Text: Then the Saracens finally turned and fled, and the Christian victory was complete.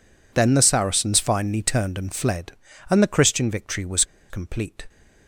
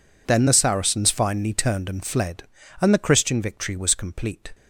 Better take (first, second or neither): second